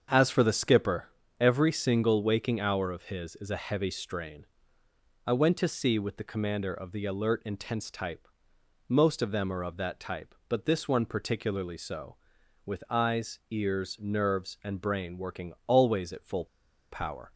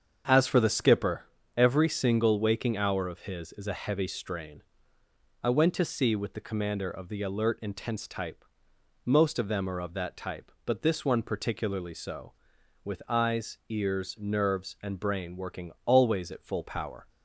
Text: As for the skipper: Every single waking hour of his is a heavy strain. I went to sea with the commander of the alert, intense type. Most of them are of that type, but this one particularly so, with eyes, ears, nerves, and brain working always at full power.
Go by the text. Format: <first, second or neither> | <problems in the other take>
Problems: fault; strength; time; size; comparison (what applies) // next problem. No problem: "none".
second | starts louder than the rest; strong; until 1.4 s; 7.5 dB; strong in the second // pauses between "full" and "power"; noticeable; at 16.4 s; 0.46 s long